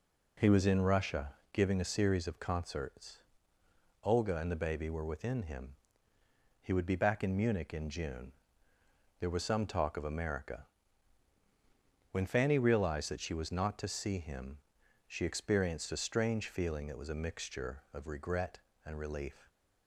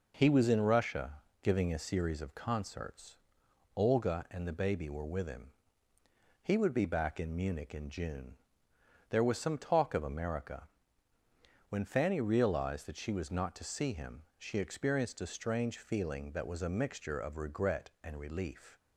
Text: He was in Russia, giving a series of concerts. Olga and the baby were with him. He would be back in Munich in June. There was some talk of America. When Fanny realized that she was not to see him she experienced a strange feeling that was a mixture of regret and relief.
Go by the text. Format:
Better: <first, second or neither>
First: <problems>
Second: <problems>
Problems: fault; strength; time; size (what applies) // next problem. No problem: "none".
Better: second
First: says "within" for "with"; at 5.0 s // pauses between "him" and "she"; noticeable; at 14.5 s; 0.52 s long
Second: pauses between "him" and "she"; slight; at 14.2 s; 0.16 s long